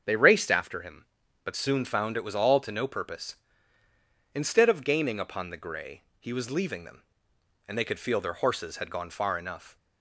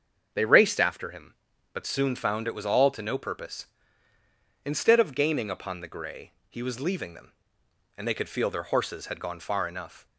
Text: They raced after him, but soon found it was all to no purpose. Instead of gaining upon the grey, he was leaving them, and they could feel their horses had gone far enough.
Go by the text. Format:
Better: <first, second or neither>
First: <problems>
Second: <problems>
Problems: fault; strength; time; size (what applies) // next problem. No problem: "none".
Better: neither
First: starts louder than the rest; until 1.0 s; 7 dB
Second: starts louder than the rest; until 1.3 s; 7 dB